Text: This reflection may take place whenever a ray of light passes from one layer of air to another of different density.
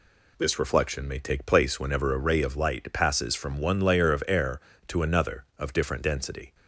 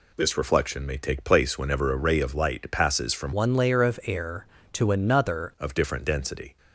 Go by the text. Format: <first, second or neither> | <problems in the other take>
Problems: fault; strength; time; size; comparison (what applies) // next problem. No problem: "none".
first | changes voice from "one" to "another"; from 3.3 to 5.5 s; 2.2 s long